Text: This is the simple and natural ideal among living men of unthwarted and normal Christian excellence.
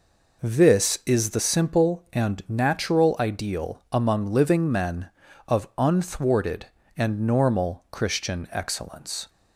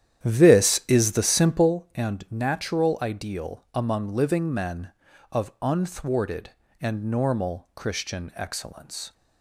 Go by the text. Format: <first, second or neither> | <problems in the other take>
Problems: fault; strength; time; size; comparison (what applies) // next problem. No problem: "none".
first | starts louder than the rest; strong; until 1.7 s; 10.5 dB